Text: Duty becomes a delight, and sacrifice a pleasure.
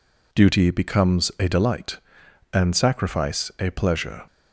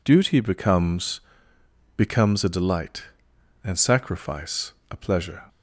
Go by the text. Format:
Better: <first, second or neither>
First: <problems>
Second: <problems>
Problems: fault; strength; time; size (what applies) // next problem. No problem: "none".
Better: first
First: none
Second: says "becomes" twice; at 1.9 s // pauses between "sacrifice" and "a"; slight; at 4.7 s; 0.18 s long